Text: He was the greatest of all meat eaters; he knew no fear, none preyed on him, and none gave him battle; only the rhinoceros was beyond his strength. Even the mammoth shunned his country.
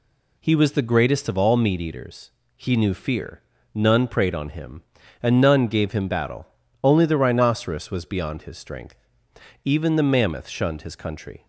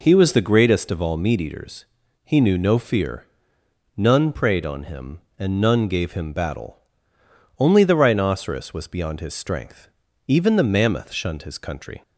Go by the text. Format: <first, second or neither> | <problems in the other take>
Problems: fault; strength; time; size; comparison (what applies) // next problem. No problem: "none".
second | skips "no"; at 2.9 s